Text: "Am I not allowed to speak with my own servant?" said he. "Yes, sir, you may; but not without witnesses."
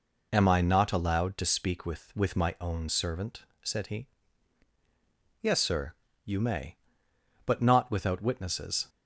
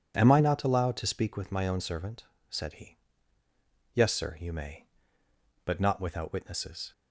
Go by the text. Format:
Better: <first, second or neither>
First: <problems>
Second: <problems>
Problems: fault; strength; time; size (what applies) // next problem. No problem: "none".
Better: second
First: says "with" twice; at 2.1 s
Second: none